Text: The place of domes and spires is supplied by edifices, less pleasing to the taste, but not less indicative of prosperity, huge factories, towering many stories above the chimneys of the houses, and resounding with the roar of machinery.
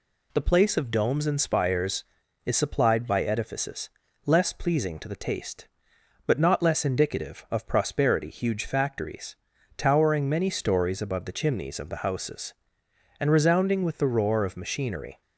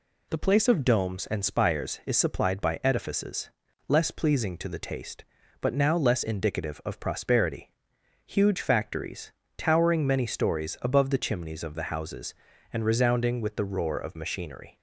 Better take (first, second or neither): first